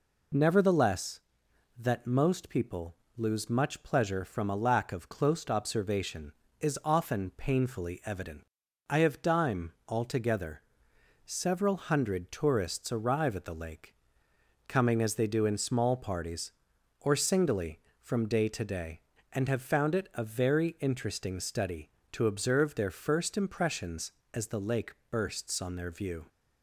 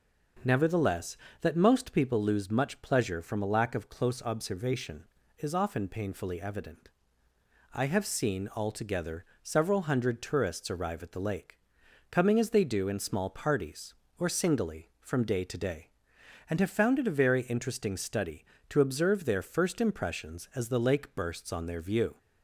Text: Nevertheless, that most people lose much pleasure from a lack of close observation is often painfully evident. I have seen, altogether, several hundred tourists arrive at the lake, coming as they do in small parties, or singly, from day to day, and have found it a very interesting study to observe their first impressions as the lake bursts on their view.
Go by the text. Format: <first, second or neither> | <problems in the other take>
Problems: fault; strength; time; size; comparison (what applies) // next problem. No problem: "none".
second | pauses between "people" and "lose"; slight; at 2.9 s; 0.22 s long // says "dime" for "seen"; at 9.2 s // pauses between "lake" and "bursts"; slight; at 24.9 s; 0.18 s long